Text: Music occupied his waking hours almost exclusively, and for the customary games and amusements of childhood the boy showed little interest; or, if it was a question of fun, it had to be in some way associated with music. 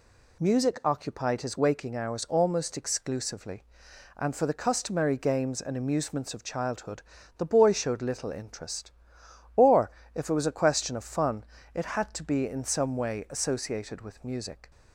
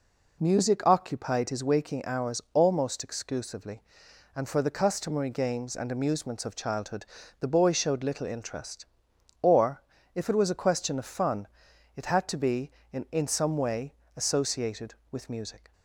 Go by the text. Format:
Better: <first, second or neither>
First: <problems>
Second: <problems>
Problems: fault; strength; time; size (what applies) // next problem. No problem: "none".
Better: first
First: pauses between "childhood" and "the"; slight; at 7.0 s; 0.36 s long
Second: pauses between "childhood" and "the"; slight; at 7.0 s; 0.36 s long // says "in" twice; at 13.0 s // pauses between "way" and "associated"; slight; at 13.9 s; 0.22 s long